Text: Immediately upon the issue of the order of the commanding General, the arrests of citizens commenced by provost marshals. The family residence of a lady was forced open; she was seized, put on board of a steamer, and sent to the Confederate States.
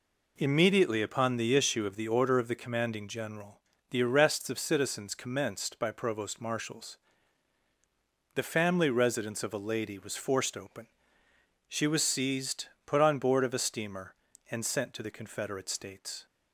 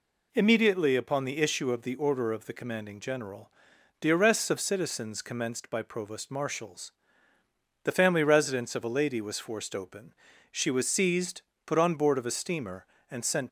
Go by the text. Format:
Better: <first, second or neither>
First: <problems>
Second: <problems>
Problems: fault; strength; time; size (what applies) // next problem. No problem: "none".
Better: first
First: none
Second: stops before "to the Confederate States"; at 13.4 s